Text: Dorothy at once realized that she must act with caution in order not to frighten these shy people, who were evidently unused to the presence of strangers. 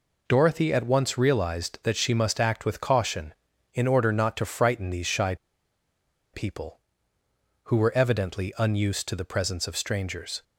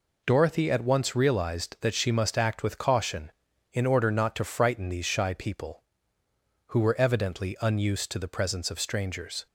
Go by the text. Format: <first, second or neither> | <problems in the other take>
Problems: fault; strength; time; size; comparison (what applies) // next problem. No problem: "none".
second | pauses between "shy" and "people"; at 5.3 s; 0.98 s long